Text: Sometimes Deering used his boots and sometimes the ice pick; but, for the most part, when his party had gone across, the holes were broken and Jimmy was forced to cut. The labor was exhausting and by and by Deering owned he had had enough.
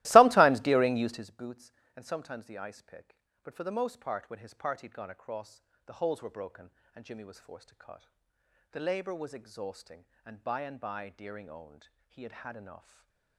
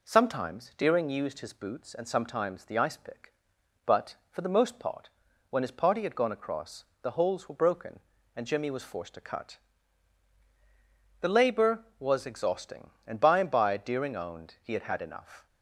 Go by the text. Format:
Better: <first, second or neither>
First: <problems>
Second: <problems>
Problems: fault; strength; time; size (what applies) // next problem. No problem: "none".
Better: second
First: starts louder than the rest; strong; until 1.3 s; 18 dB // pauses between "owned" and "he"; slight; at 11.8 s; 0.20 s long // stays silent after the last word; slight; from 12.7 s on; 0.6 s long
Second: none